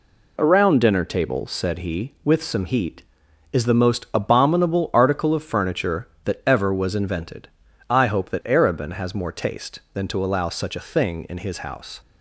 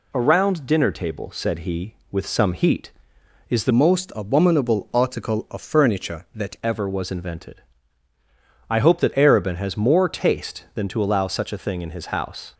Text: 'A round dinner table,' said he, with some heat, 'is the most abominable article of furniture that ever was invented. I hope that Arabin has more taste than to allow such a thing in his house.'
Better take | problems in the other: first | changes voice from "most" to "that"; from 3.7 to 6.5 s; 2.8 s long

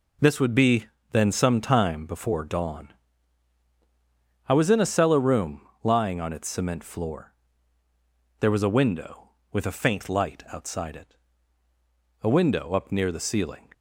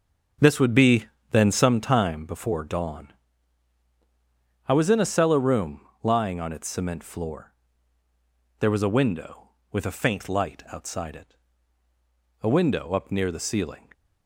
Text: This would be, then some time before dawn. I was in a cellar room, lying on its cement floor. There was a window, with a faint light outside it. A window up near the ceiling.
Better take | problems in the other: first | starts louder than the rest; until 1.7 s; 6.5 dB

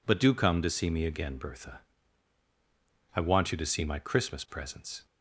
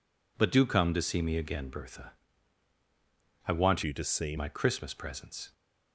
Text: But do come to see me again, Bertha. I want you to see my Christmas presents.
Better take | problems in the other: first | changes voice from "you" to "see"; from 3.8 to 4.3 s; 0.5 s long

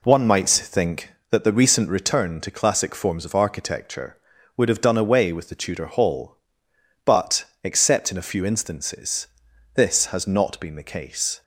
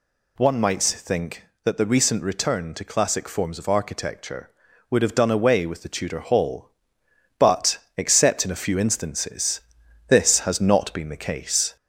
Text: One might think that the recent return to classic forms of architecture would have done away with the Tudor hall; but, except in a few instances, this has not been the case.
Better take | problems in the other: first | gets louder; slight; throughout; 2.5 dB

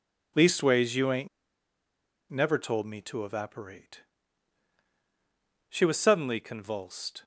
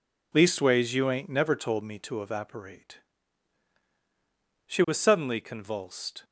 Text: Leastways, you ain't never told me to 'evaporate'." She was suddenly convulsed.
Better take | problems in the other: second | pauses between "ain't" and "never"; at 1.2 s; 1.0 s long

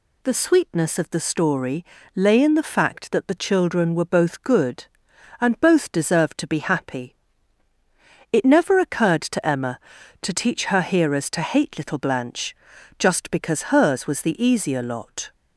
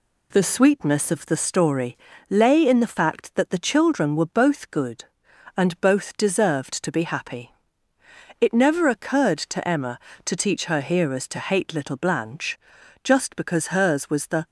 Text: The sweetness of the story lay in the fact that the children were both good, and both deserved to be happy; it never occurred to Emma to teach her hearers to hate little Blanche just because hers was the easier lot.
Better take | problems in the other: first | pauses between "story" and "lay"; slight; at 1.9 s; 0.32 s long; slight in the first // pauses between "Blanche" and "just"; noticeable; at 12.5 s; 0.46 s long; also in the first // stops before "easier lot"; at 14.4 s

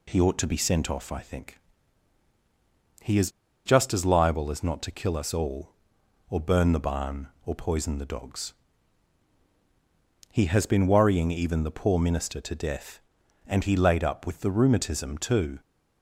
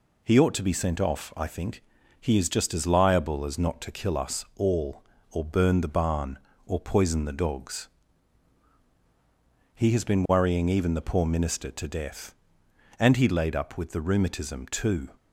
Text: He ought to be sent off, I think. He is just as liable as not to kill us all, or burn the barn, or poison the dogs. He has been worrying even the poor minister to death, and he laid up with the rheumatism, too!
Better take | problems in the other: second | pauses between "is" and "just"; at 3.2 s; 0.36 s long

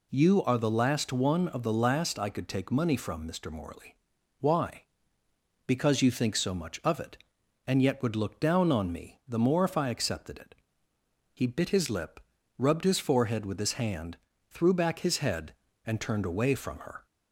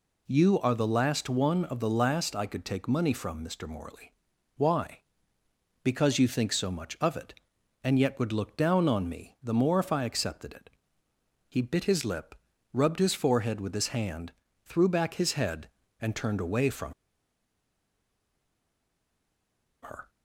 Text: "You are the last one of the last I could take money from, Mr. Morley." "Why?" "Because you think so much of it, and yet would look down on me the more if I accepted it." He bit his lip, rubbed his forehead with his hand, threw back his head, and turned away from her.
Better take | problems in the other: first | pauses between "from" and "her"; strong; at 16.9 s; 2.8 s long

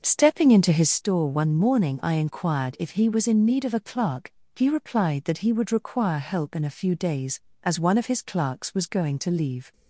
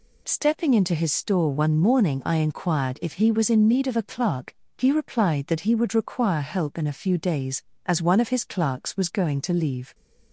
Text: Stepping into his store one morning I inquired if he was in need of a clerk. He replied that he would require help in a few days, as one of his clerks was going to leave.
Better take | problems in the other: second | starts louder than the rest; noticeable; until 1.0 s; 6 dB

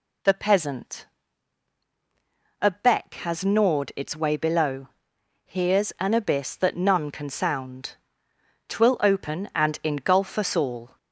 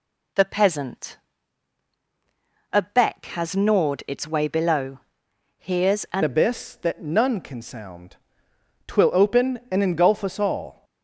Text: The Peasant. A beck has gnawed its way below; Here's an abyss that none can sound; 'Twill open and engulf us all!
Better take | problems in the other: first | changes voice at "abyss"; from 6.2 s on; 4.6 s long

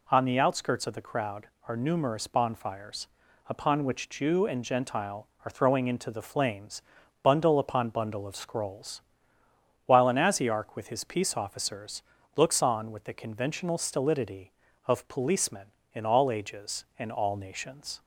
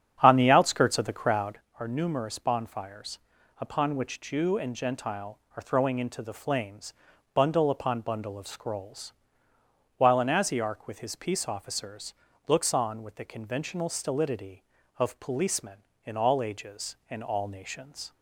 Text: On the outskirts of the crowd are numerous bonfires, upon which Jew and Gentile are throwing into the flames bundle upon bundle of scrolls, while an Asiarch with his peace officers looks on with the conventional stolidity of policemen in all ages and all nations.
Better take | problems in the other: first | starts louder than the rest; strong; until 1.6 s; 8.5 dB // pauses between "flames" and "bundle"; at 6.9 s; 0.40 s long; also in the first // pauses between "officers" and "looks"; slight; at 12.1 s; 0.32 s long; slight in the first

